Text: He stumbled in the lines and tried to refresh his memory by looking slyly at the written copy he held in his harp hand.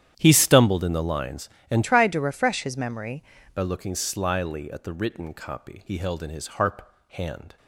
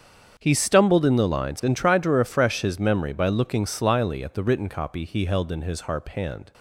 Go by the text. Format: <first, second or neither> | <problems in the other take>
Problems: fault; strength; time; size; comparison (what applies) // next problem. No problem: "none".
second | starts louder than the rest; strong; until 1.1 s; 10 dB; strong in the second // changes voice from "tried" to "memory"; from 1.8 to 3.2 s; 1.4 s long // pauses between "harp" and "hand"; slight; at 6.8 s; 0.26 s long